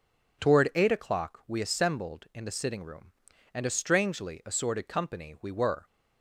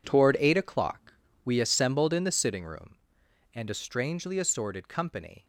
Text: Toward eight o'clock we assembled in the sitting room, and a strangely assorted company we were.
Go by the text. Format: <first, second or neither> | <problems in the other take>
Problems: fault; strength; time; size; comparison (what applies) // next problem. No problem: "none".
first | pauses between "o'clock" and "we"; slight; at 1.1 s; 0.32 s long // stops before "we were"; at 5.4 s